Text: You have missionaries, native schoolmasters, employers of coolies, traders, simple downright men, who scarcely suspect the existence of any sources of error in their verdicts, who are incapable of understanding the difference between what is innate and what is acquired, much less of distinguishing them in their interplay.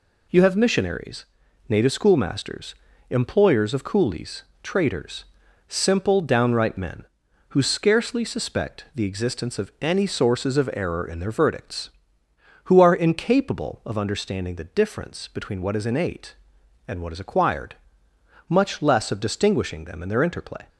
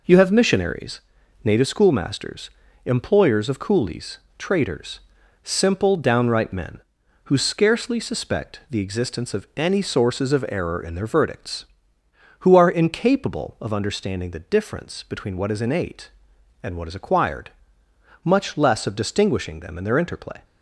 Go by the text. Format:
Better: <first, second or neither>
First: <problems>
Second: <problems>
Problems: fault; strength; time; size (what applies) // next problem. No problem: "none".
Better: first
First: none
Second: starts louder than the rest; noticeable; until 1.6 s; 4.5 dB